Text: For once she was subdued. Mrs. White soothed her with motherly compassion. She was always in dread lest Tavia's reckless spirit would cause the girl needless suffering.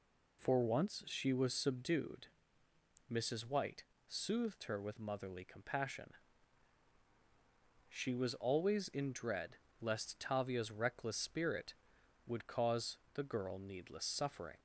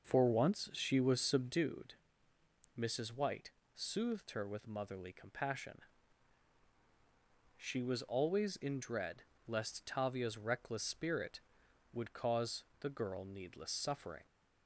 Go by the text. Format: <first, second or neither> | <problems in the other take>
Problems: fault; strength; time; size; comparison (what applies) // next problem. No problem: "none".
first | starts louder than the rest; noticeable; until 1.6 s; 5.5 dB // pauses between "White" and "soothed"; slight; at 3.4 s; 0.24 s long; slight in the first // pauses between "dread" and "lest"; slight; at 9.2 s; 0.24 s long; slight in the first // pauses between "cause" and "the"; slight; at 12.6 s; 0.16 s long; slight in the first